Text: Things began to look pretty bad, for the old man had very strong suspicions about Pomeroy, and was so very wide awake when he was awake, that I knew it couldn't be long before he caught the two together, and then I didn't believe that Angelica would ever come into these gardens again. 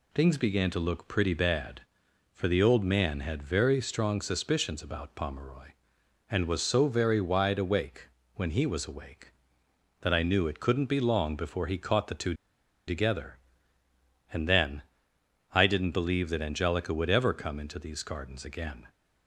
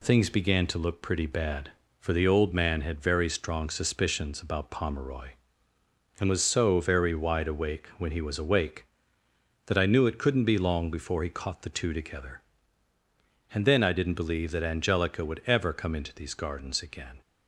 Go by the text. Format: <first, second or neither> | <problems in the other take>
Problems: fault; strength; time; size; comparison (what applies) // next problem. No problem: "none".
second | pauses between "awake" and "when"; slight; at 8.0 s; 0.26 s long // pauses between "two" and "together"; noticeable; at 12.3 s; 0.54 s long // pauses between "then" and "I"; noticeable; at 14.8 s; 0.70 s long